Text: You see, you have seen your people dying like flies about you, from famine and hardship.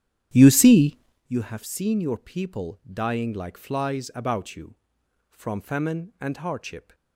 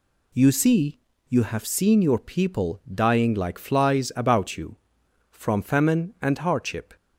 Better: second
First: starts louder than the rest; strong; until 1.3 s; 10 dB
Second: none

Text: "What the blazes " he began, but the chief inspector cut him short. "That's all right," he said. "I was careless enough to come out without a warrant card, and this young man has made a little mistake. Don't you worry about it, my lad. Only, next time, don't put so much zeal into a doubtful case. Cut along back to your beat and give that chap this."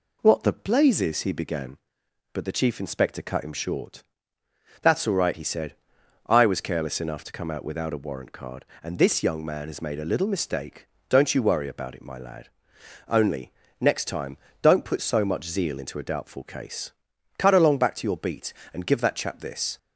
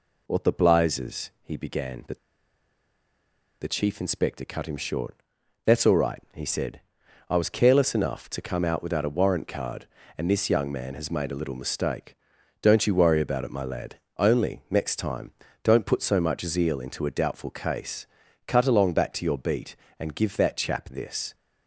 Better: first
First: none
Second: pauses between "but" and "the"; strong; at 2.1 s; 1.4 s long

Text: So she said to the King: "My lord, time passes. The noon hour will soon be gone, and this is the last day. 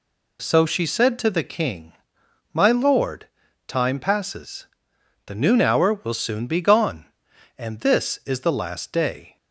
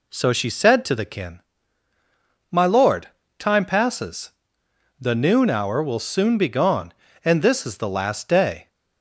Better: first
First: none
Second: says "Kin" for "King"; at 1.0 s

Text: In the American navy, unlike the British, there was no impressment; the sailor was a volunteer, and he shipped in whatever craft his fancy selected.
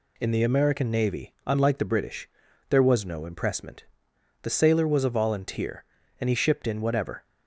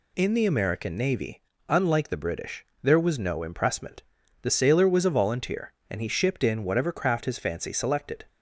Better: second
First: stops before "craft his fancy selected"; at 7.2 s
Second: none

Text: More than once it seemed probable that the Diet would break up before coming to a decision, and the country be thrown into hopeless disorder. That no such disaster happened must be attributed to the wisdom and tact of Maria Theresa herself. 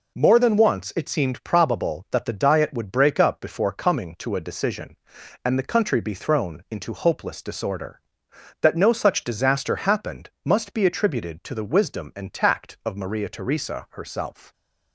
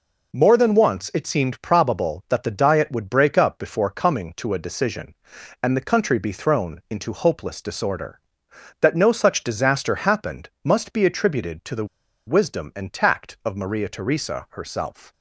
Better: first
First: pauses between "happened" and "must"; slight; at 10.2 s; 0.16 s long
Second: pauses between "happened" and "must"; slight; at 10.4 s; 0.16 s long // pauses between "the" and "wisdom"; at 11.8 s; 0.41 s long

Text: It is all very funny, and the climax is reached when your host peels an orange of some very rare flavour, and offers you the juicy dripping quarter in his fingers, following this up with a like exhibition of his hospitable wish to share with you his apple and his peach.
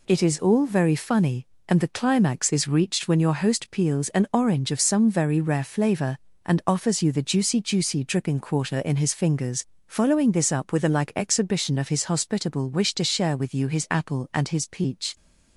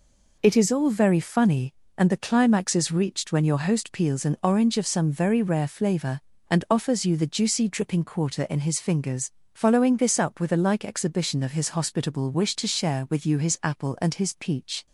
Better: second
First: says "juicy" twice; at 7.5 s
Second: none

